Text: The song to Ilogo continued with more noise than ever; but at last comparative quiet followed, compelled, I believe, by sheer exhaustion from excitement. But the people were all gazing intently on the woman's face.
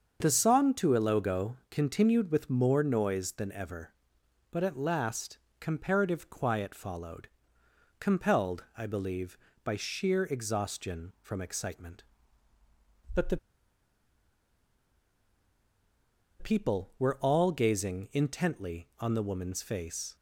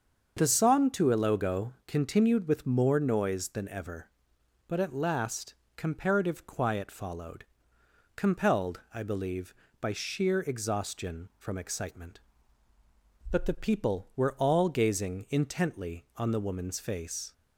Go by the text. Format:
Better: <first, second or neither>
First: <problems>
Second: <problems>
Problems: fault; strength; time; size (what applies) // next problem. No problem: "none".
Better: second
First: starts louder than the rest; until 1.2 s; 7 dB // pauses between "Ilogo" and "continued"; slight; at 1.5 s; 0.16 s long // pauses between "last" and "comparative"; slight; at 5.3 s; 0.20 s long // pauses between "the" and "people"; strong; at 13.3 s; 3.0 s long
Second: starts louder than the rest; until 1.3 s; 7 dB // pauses between "Ilogo" and "continued"; slight; at 1.7 s; 0.16 s long // pauses between "last" and "comparative"; slight; at 5.5 s; 0.20 s long